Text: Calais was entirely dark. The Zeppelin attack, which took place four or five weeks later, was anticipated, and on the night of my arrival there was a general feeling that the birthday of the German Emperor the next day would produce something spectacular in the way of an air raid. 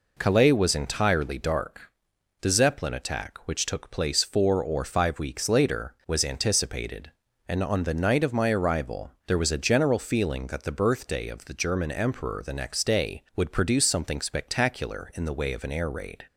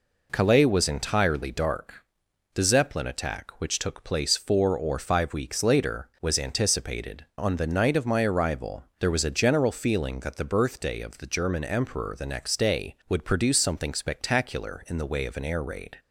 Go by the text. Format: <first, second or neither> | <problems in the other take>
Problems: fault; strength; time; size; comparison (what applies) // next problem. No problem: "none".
first | skips "and"; at 7.3 s // pauses between "arrival" and "there"; slight; at 8.8 s; 0.16 s long; slight in the first